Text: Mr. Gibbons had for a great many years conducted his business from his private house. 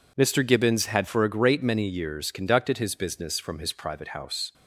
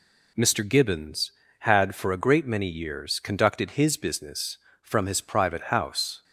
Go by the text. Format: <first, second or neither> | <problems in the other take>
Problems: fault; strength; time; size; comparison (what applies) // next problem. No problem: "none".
neither | none